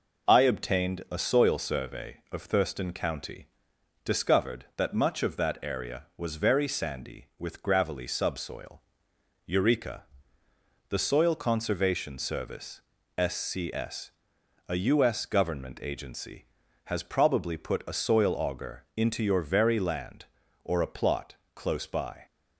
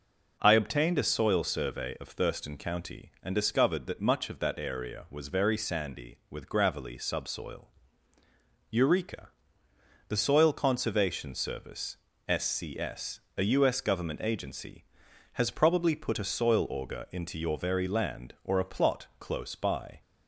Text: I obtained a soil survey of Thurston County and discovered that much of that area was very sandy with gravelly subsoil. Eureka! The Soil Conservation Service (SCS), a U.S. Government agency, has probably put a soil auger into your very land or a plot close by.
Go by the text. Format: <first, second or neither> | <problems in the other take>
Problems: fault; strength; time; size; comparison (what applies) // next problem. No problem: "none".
second | skips "and"; at 3.7 s // pauses between "plot" and "close"; slight; at 21.3 s; 0.18 s long